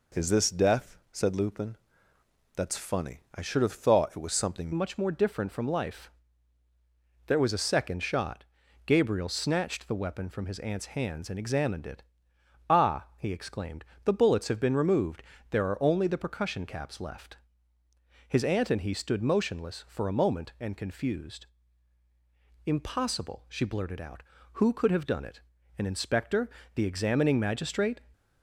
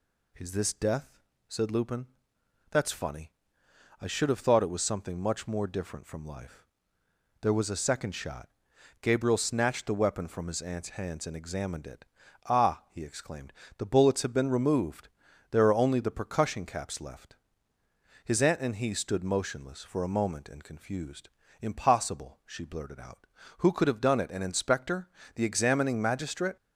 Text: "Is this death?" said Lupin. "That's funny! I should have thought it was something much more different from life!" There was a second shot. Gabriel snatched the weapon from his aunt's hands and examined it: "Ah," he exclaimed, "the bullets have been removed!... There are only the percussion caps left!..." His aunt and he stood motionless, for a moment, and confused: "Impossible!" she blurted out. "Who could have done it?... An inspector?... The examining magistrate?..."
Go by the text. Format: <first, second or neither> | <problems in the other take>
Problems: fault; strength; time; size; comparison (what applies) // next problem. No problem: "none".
second | changes voice at "much"; from 4.7 s on; 23.3 s long